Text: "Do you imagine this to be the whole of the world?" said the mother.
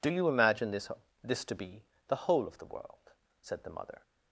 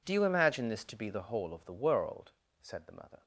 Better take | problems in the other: second | says "this" twice; at 1.2 s // pauses between "be" and "the"; slight; at 1.8 s; 0.26 s long

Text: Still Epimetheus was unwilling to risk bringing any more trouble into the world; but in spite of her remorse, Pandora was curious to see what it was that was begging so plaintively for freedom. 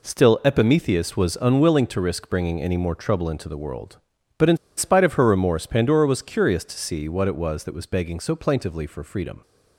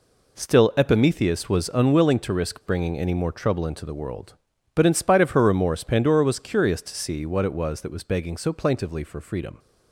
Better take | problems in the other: second | pauses between "in" and "spite"; slight; at 4.5 s; 0.19 s long

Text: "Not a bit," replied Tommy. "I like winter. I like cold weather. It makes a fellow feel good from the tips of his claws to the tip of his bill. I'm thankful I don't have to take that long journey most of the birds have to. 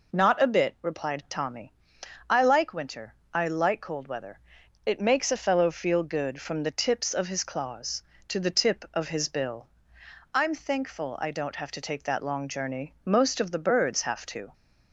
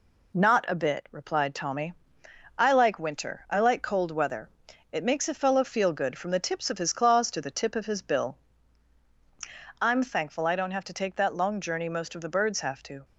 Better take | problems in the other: first | gets quieter; slight; throughout; 3 dB

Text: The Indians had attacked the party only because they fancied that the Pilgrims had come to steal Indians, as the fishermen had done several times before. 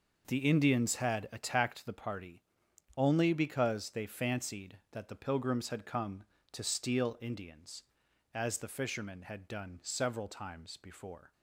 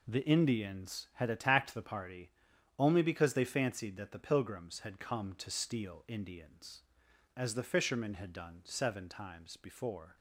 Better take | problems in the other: first | pauses between "party" and "only"; noticeable; at 2.3 s; 0.46 s long; noticeable in the first // says "seven" for "several"; at 8.6 s

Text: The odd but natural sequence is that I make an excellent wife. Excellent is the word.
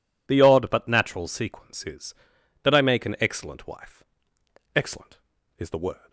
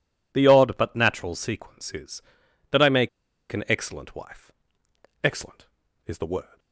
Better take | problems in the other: first | pauses between "make" and "an"; at 3.0 s; 0.43 s long

